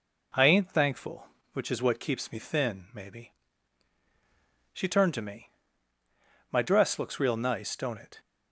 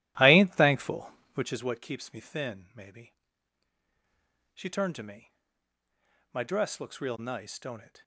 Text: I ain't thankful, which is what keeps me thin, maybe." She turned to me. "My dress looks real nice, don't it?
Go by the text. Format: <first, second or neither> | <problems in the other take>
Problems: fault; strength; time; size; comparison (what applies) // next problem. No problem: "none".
first | starts louder than the rest; strong; until 1.6 s; 14.5 dB